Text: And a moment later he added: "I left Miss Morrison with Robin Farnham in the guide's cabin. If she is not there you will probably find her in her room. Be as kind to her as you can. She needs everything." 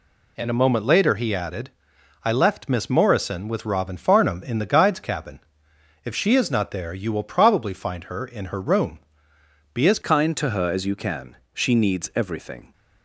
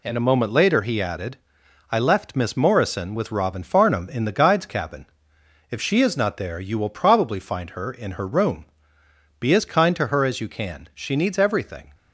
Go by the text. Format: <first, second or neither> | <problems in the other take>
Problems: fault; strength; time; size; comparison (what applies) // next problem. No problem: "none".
second | changes voice at "kind"; from 10.0 s on; 2.7 s long